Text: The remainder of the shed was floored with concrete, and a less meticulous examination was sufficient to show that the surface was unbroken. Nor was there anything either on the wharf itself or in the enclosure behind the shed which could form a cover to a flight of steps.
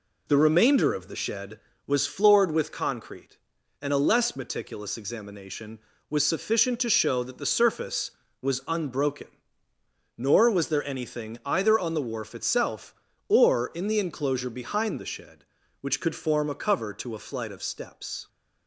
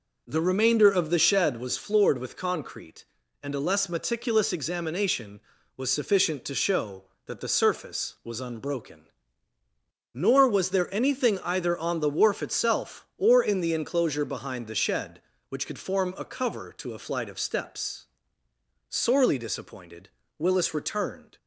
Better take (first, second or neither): first